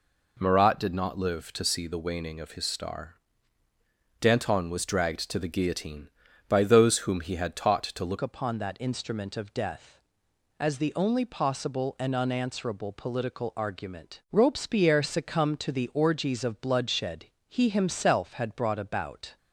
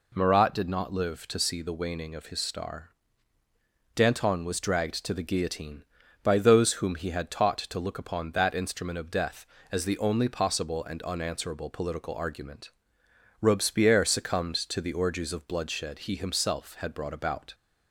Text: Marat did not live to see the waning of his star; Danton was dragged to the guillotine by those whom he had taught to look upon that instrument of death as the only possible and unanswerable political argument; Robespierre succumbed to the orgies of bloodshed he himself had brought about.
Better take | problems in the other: second | changes voice at "upon"; from 8.2 s on; 11.1 s long // pauses between "bloodshed" and "he"; slight; at 17.2 s; 0.20 s long

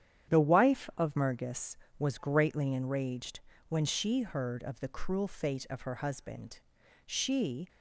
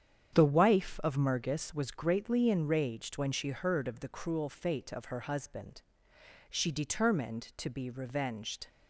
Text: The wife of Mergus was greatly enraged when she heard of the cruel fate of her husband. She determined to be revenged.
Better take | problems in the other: second | starts louder than the rest; strong; until 1.3 s; 9.5 dB; strong in the second // pauses between "enraged" and "when"; slight; at 3.3 s; 0.30 s long // stops before "determined to be revenged"; at 7.6 s

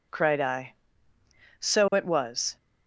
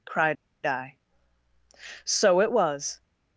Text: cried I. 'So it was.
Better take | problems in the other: first | pauses between "cried" and "I"; slight; at 0.3 s; 0.30 s long

